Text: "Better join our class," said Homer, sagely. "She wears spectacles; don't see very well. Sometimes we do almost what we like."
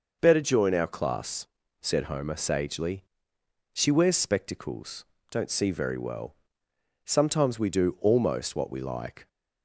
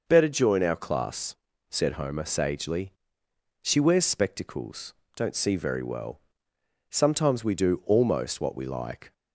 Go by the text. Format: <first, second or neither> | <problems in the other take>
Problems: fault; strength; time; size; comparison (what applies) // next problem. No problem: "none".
neither | none